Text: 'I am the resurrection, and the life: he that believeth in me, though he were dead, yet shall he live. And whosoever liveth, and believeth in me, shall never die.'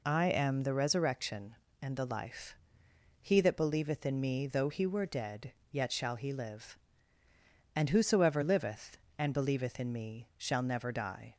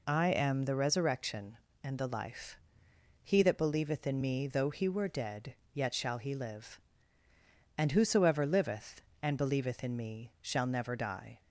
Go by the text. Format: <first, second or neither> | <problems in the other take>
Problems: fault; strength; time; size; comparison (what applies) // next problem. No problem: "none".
neither | none